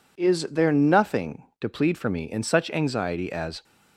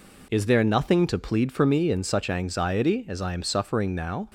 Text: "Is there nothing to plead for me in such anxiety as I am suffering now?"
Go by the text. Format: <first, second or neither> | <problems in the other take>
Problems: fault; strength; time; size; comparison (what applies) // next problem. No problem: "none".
second | stops before "I am suffering now"; at 3.6 s